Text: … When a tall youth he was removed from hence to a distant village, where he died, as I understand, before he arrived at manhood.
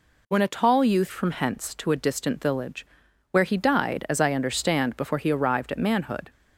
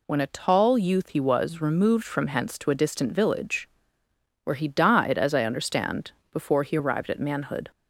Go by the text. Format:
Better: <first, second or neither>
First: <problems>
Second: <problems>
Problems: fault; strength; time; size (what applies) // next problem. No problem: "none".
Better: second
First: skips "he was removed"; at 1.1 s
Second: none